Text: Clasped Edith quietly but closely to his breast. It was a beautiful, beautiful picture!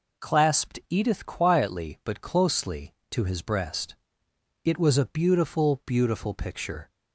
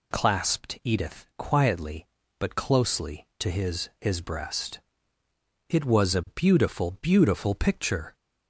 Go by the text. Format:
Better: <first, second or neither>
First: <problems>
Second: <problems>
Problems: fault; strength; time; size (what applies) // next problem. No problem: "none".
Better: first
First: none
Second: says "his" twice; at 3.9 s